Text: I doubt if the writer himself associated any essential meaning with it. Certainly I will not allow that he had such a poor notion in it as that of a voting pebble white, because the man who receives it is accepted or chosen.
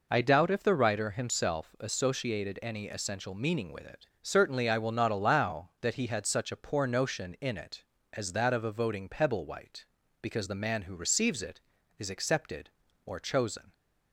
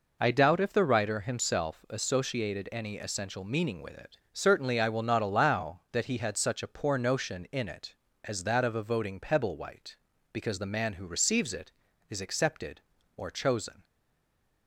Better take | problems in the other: first | stays silent after the last word; slight; from 13.8 s on; 0.8 s long

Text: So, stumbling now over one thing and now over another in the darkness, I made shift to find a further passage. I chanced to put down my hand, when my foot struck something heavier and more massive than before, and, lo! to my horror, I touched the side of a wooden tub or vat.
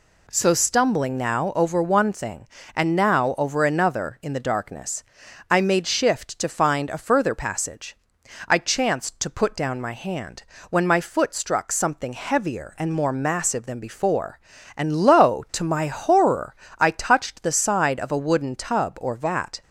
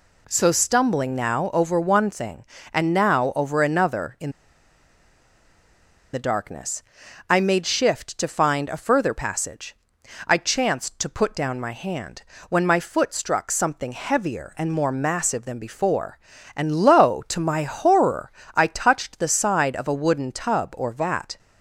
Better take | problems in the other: first | pauses between "in" and "the"; strong; at 4.3 s; 1.8 s long

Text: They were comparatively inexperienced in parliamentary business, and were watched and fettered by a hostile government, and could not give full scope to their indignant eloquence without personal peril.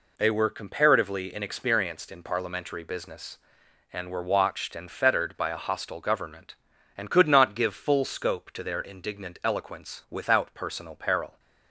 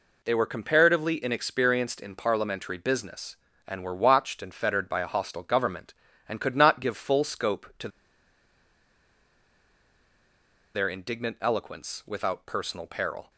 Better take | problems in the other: first | pauses between "to" and "their"; strong; at 7.8 s; 2.8 s long

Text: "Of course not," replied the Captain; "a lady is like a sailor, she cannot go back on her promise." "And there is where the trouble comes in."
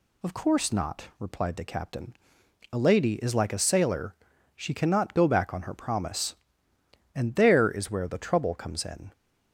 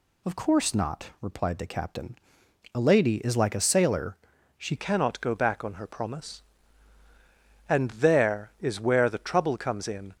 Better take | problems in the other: first | changes voice at "cannot"; from 4.7 s on; 5.4 s long

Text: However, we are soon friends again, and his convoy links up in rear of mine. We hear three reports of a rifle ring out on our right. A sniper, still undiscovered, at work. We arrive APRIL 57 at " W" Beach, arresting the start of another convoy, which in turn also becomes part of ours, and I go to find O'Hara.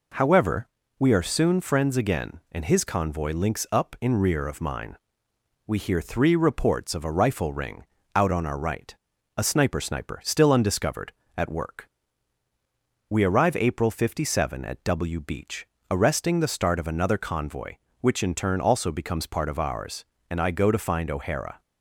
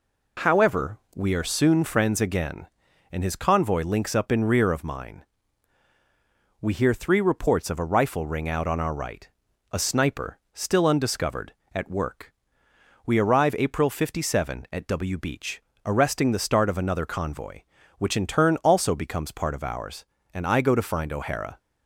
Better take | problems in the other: second | pauses between "ring" and "out"; slight; at 7.8 s; 0.30 s long // says "sniper" twice; at 9.8 s

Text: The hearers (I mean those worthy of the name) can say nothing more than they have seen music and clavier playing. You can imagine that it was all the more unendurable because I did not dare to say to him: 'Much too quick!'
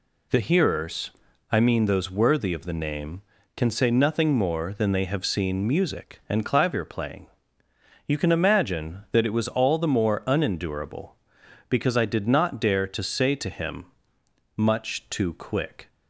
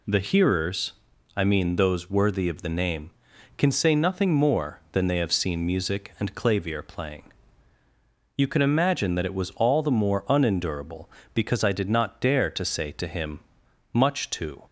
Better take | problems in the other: first | stops before "quick"; at 14.6 s

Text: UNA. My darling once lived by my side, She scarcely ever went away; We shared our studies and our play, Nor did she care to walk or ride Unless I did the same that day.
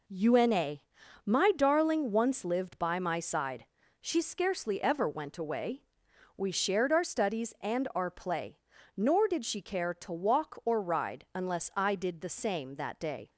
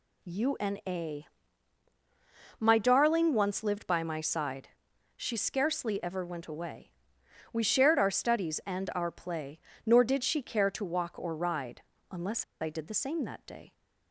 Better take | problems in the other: first | pauses between "ride" and "Unless"; slight; at 11.8 s; 0.30 s long // pauses between "Unless" and "I"; slight; at 12.4 s; 0.17 s long

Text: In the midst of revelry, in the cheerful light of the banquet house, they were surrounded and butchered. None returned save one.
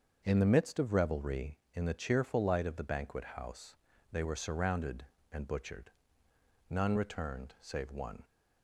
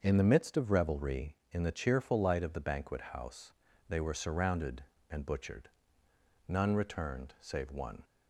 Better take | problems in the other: neither | starts louder than the rest; the same in both

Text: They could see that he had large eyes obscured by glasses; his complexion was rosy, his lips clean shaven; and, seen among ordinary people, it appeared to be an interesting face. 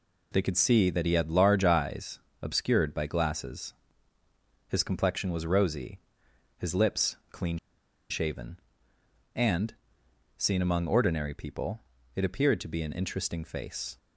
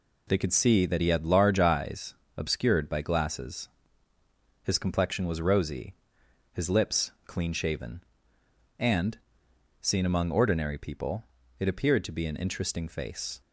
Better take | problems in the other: second | pauses between "eyes" and "obscured"; slight; at 2.1 s; 0.22 s long; slight in the second // pauses between "lips" and "clean"; slight; at 7.1 s; 0.16 s long; slight in the second // pauses between "clean" and "shaven"; noticeable; at 7.5 s; 0.51 s long

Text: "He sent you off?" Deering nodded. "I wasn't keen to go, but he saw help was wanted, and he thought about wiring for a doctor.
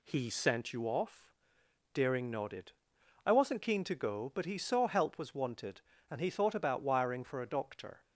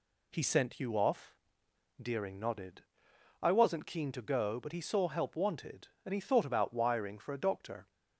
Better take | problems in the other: first | skips "was"; at 5.3 s

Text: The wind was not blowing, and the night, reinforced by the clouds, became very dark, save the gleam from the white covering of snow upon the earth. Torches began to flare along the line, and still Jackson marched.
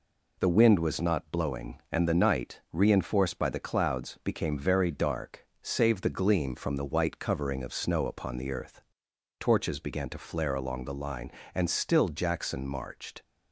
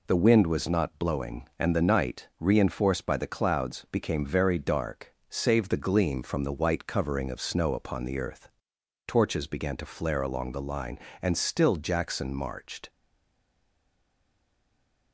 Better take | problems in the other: first | stays silent after the last word; from 12.8 s on; 2.3 s long

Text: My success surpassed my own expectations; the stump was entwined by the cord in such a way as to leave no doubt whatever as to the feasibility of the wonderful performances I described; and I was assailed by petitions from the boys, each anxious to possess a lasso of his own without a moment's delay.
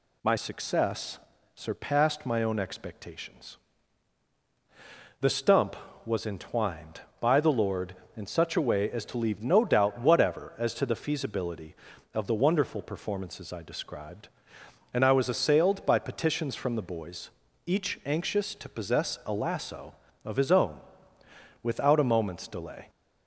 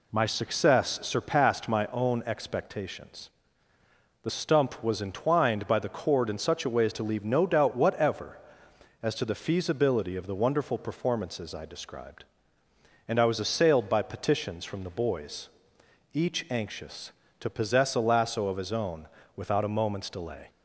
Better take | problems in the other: second | pauses between "success" and "surpassed"; slight; at 1.1 s; 0.36 s long // says "lord" for "cord"; at 7.5 s // pauses between "own" and "without"; noticeable; at 20.8 s; 0.82 s long; slight in the second

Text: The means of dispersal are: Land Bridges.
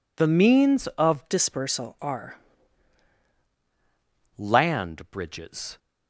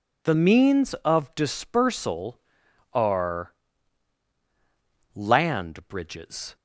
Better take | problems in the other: second | changes voice from "dispersal" to "are"; from 1.3 to 2.3 s; 1.0 s long

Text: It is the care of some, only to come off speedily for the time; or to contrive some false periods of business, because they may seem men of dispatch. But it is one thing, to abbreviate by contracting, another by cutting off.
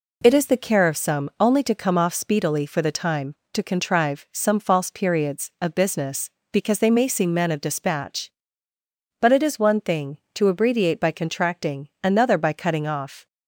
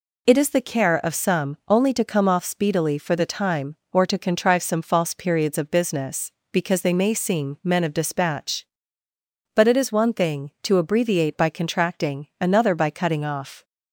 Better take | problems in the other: second | skips "or"; at 3.4 s

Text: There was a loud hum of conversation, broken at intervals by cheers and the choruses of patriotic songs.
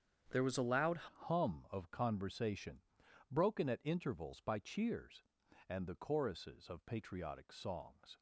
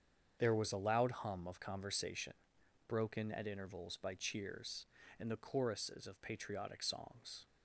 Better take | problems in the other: second | starts louder than the rest; strong; until 1.4 s; 8 dB; strong in the second // changes voice at "hum"; from 1.0 s on; 7.1 s long

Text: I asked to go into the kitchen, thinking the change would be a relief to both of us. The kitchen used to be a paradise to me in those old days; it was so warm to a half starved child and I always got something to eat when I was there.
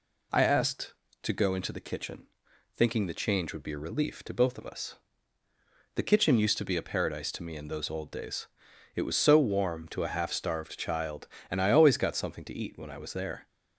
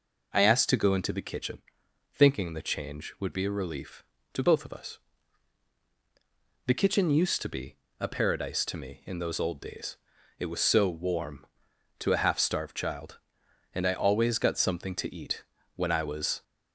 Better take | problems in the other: first | pauses between "be" and "a"; slight; at 7.7 s; 0.22 s long // pauses between "eat" and "when"; slight; at 15.4 s; 0.30 s long // stops before "there"; at 16.4 s

